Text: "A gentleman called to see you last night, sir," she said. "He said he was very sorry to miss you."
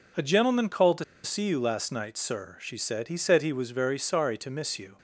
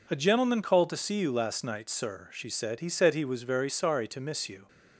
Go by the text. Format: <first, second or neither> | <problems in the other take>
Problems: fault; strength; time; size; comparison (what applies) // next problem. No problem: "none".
second | pauses between "to" and "see"; slight; at 1.0 s; 0.21 s long